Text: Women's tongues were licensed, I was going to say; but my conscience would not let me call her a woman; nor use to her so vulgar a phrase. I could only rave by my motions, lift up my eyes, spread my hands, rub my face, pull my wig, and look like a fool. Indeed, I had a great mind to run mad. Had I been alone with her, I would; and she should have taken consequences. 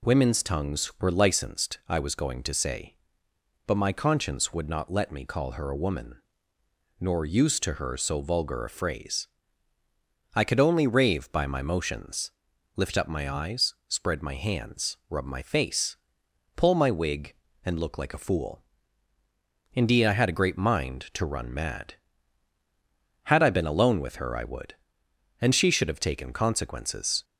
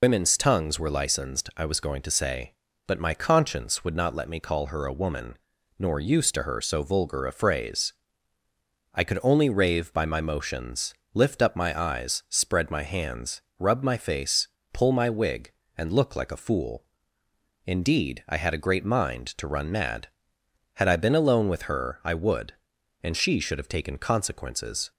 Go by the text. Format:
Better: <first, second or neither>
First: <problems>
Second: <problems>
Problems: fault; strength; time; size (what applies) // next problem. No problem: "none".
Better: first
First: none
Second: loses the start of "Women's"; at 0.0 s; 95 ms